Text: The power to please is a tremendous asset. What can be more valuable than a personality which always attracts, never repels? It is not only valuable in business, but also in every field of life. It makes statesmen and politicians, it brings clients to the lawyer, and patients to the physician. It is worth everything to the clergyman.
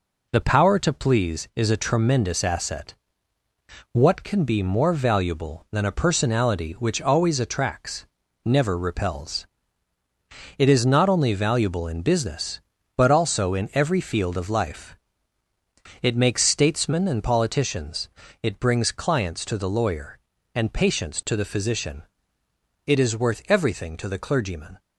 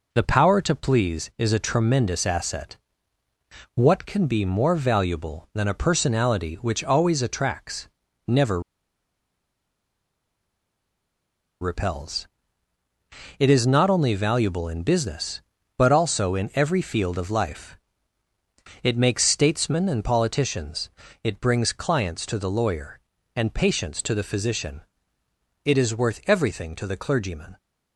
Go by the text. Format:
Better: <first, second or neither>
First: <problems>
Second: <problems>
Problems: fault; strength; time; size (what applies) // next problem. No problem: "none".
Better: first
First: none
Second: pauses between "never" and "repels"; strong; at 8.6 s; 3.0 s long